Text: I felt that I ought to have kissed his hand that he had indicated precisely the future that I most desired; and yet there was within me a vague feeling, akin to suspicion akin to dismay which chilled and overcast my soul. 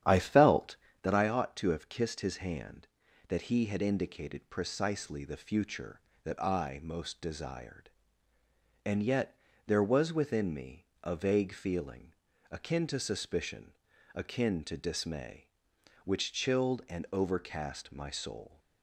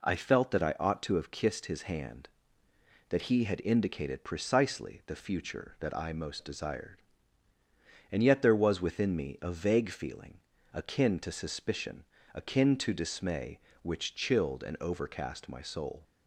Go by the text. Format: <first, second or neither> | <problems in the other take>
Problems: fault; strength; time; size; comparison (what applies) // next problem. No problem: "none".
second | starts louder than the rest; strong; until 1.1 s; 10 dB // pauses between "yet" and "there"; slight; at 9.3 s; 0.30 s long // pauses between "me" and "a"; slight; at 10.8 s; 0.18 s long // pauses between "suspicion" and "akin"; slight; at 13.7 s; 0.36 s long; slight in the second